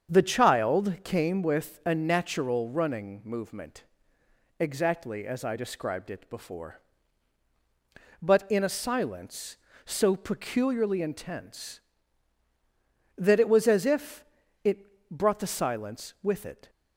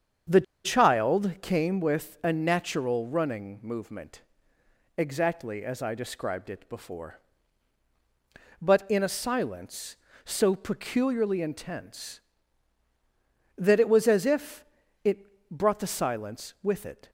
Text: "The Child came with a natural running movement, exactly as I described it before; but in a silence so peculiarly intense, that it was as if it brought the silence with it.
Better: first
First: starts louder than the rest; strong; until 1.1 s; 7.5 dB // pauses between "if" and "it"; at 14.2 s; 0.40 s long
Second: starts louder than the rest; strong; until 1.5 s; 7.5 dB // pauses between "The" and "Child"; slight; at 0.4 s; 0.22 s long // pauses between "if" and "it"; at 14.6 s; 0.40 s long

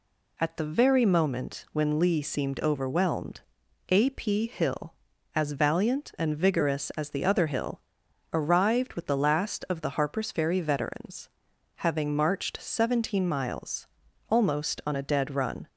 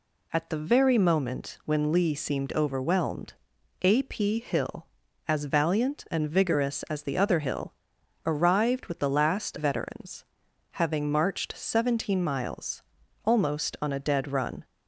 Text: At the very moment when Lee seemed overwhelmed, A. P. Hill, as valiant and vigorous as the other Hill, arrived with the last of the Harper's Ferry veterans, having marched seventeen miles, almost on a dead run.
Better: first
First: none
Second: skips "of the Harper's Ferry"; at 9.5 s

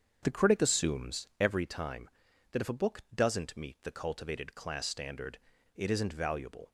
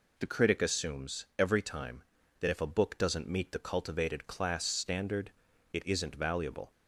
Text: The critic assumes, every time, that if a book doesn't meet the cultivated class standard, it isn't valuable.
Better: second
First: starts louder than the rest; strong; until 1.5 s; 7 dB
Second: none

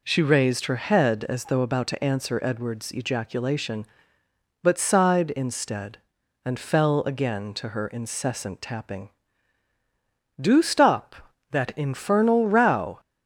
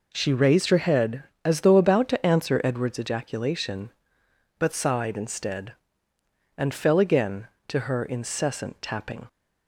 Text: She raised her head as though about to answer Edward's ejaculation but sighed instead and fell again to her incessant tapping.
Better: second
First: goes on to say "Do stop that infernal row"; strong; from 10.3 s on; 2.6 s long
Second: none

